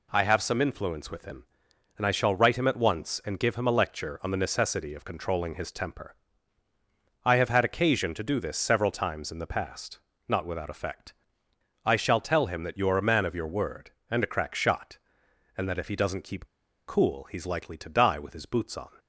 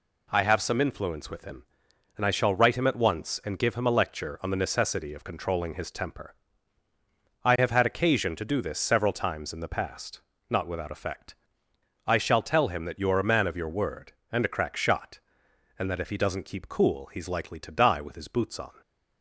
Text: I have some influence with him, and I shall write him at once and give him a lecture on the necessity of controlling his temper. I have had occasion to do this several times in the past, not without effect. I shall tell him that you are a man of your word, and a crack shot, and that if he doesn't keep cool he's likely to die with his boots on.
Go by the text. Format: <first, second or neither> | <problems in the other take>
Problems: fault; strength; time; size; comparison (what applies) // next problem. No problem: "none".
second | pauses between "keep" and "cool"; at 16.4 s; 0.39 s long